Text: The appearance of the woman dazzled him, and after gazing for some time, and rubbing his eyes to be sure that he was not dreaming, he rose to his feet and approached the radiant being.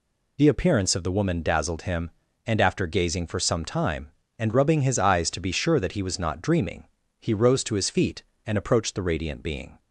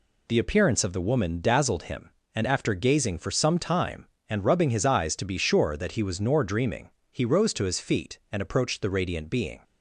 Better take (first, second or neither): first